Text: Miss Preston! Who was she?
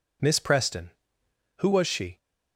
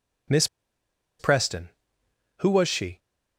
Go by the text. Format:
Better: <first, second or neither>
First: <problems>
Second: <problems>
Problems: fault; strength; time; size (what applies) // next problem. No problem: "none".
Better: first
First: none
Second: pauses between "Miss" and "Preston"; noticeable; at 0.4 s; 0.73 s long